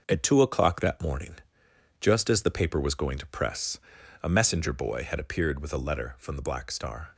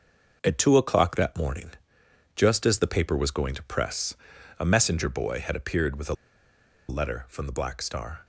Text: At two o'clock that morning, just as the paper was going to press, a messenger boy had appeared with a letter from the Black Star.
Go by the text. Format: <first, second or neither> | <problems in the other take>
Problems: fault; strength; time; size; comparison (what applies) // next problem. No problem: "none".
first | starts louder than the rest; until 1.4 s; 6 dB; noticeable in the first // pauses between "a" and "letter"; noticeable; at 6.1 s; 0.75 s long